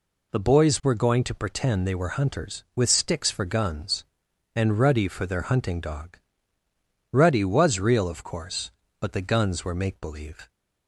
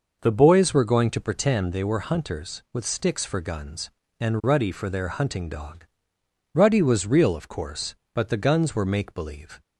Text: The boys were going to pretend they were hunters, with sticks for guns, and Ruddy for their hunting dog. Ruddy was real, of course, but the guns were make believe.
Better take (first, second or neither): neither